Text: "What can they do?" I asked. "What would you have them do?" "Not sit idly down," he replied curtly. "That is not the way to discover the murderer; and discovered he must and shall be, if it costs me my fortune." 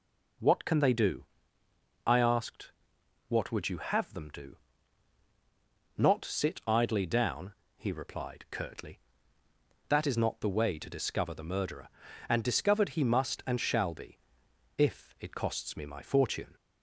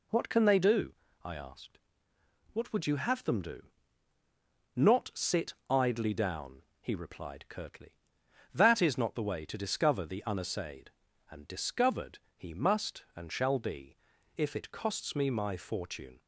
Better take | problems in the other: first | pauses between "sit" and "idly"; slight; at 5.5 s; 0.16 s long // says "unassayed" for "murderer"; at 10.2 s // pauses between "discovered" and "he"; slight; at 12.1 s; 0.18 s long

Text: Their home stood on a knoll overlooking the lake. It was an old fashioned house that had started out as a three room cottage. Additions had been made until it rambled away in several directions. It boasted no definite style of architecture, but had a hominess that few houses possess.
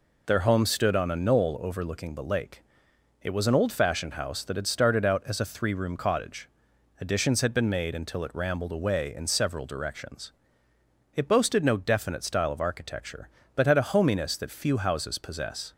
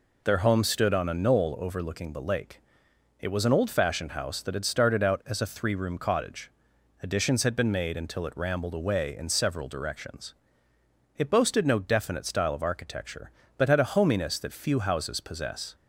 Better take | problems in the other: neither | none

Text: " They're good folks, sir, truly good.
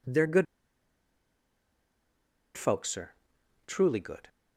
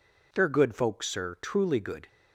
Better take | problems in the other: second | pauses between "good" and "folks"; strong; at 0.4 s; 2.1 s long

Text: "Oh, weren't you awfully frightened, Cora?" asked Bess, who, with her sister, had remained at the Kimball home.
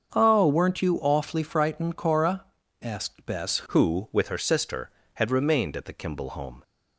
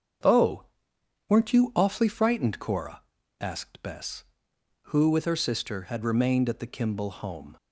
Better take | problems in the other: second | starts louder than the rest; until 1.1 s; 7 dB; strong in the second // changes voice at "who"; from 3.6 s on; 3.0 s long

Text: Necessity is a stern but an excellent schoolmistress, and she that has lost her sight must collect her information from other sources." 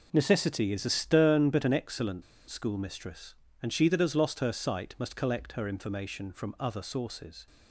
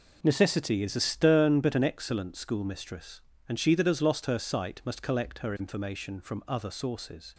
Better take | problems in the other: second | pauses between "excellent" and "schoolmistress"; slight; at 2.2 s; 0.27 s long

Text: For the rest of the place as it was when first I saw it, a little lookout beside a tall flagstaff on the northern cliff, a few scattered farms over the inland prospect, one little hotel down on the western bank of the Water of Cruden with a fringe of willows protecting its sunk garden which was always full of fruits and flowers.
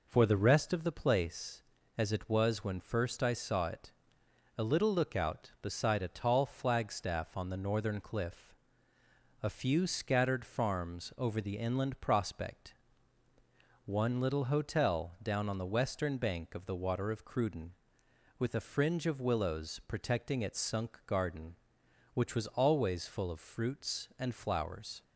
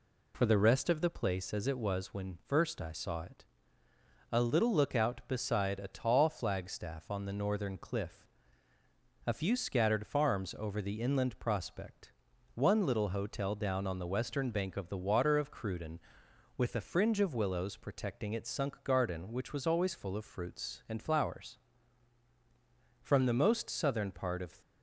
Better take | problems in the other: first | goes on to say "From the most southern part of"; from 23.0 s on; 1.5 s long

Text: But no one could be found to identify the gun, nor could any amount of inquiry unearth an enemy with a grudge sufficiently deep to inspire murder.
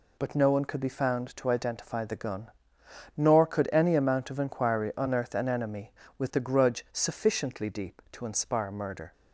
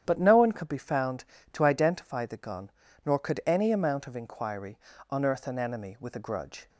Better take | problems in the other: first | starts louder than the rest; strong; until 1.0 s; 9.5 dB // pauses between "inquiry" and "unearth"; slight; at 4.7 s; 0.32 s long // stops before "sufficiently deep to inspire murder"; at 6.6 s

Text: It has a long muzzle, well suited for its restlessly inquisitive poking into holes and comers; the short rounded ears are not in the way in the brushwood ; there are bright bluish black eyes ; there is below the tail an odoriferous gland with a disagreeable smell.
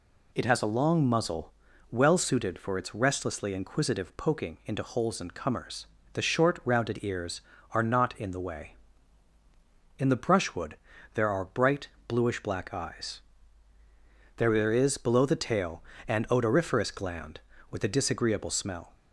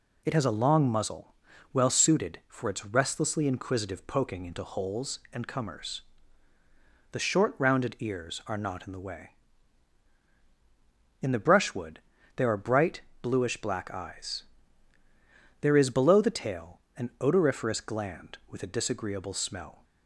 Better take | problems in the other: neither | pauses between "bright" and "bluish"; slight; the same in both // pauses between "tail" and "an"; slight; the same in both

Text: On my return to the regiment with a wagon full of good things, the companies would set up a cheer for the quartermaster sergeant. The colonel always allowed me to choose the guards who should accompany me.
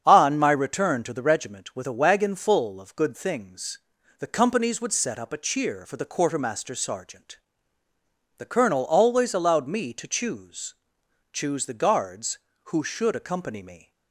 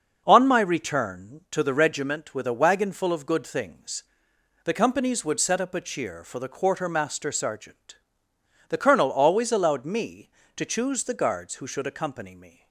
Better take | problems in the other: second | starts louder than the rest; strong; until 1.0 s; 7.5 dB; noticeable in the second // says "choose" twice; at 11.3 s

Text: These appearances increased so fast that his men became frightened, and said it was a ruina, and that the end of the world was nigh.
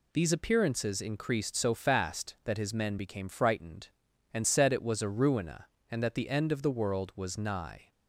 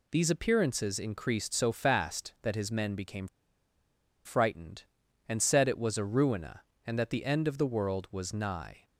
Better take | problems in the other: first | pauses between "became" and "frightened"; at 3.2 s; 0.98 s long

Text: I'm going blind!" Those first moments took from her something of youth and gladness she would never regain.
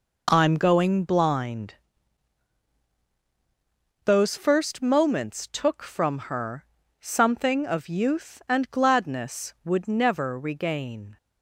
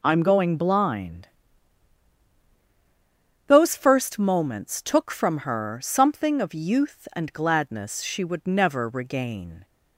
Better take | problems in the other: second | pauses between "her" and "something"; slight; at 6.6 s; 0.36 s long // skips "she"; at 9.5 s

